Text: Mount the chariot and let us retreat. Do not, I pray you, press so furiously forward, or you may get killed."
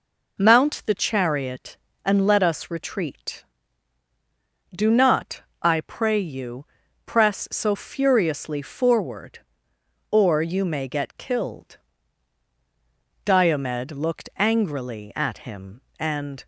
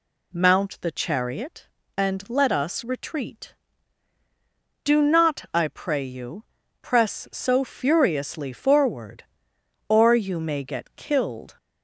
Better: second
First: goes on to say "Diomed looked angrily at him and"; strong; from 13.2 s on; 3.2 s long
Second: none

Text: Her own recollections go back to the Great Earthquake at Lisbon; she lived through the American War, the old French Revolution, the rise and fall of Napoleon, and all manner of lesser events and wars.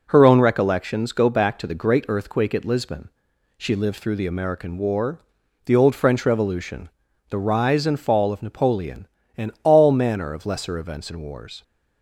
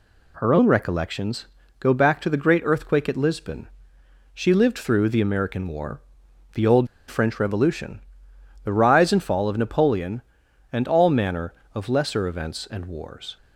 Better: first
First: none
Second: pauses between "recollections" and "go"; slight; at 1.4 s; 0.34 s long // pauses between "old" and "French"; slight; at 6.8 s; 0.22 s long

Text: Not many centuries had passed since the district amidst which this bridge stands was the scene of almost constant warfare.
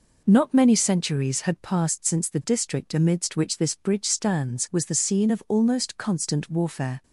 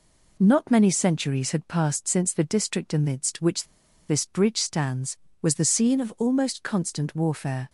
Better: first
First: none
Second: pauses between "which" and "this"; at 3.6 s; 0.45 s long

